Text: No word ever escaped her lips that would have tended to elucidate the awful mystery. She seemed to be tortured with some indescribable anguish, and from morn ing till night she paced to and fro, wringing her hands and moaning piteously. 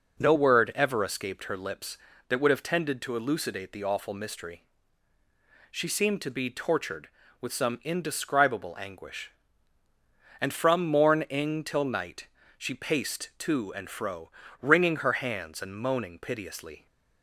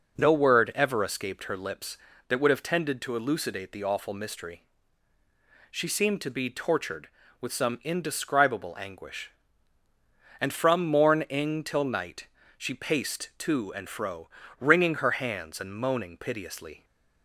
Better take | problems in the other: neither | pauses between "night" and "she"; slight; the same in both

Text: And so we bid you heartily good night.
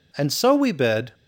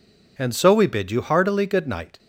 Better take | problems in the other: second | stops before "you heartily good night"; at 1.1 s

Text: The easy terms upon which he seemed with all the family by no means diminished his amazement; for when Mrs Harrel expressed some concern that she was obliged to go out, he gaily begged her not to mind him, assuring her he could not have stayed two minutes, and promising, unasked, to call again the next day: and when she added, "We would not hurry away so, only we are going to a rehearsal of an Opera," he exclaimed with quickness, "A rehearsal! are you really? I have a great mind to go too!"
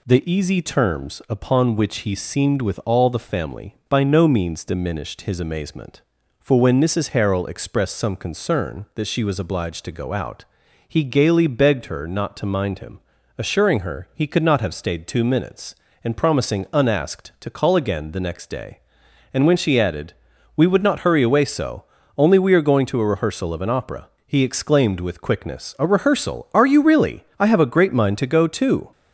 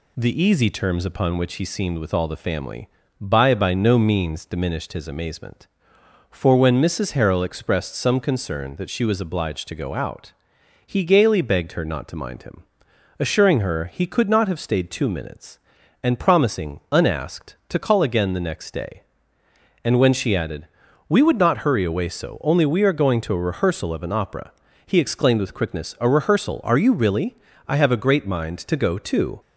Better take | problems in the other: first | says "by" twice; at 3.5 s

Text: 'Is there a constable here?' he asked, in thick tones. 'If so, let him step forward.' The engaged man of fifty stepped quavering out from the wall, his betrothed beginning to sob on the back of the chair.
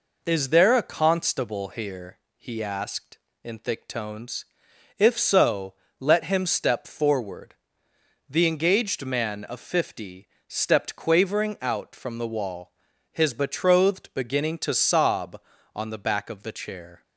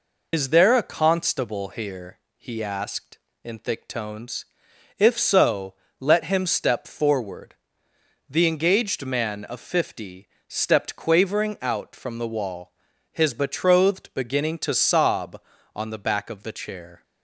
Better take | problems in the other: first | loses the start of "Is"; at 0.3 s; 90 ms // pauses between "fifty" and "stepped"; slight; at 10.2 s; 0.18 s long; slight in the first

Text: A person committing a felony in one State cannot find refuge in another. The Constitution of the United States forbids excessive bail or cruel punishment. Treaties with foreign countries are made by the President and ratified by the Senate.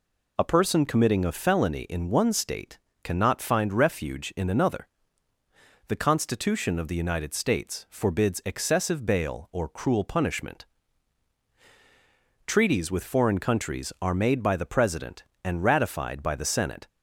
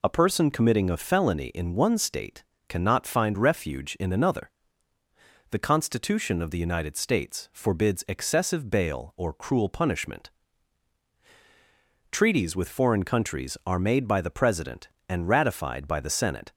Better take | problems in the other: neither | pauses between "State" and "cannot"; slight; the same in both

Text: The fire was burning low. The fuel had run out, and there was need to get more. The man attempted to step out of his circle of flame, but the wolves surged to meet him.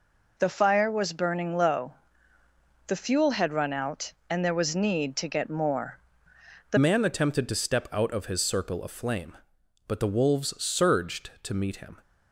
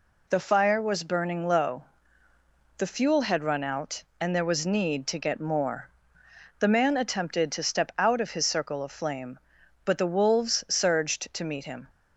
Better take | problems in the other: second | changes voice at "man"; from 6.7 s on; 5.2 s long

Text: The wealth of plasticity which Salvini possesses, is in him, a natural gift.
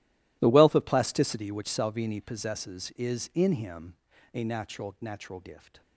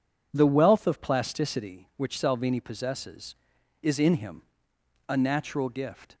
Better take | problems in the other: second | says "natural" twice; at 5.0 s

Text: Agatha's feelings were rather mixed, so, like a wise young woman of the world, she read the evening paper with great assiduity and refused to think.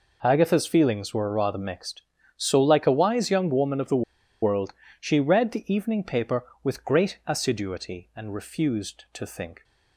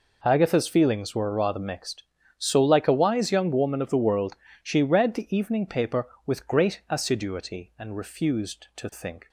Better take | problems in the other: second | pauses between "the" and "world"; at 4.0 s; 0.39 s long

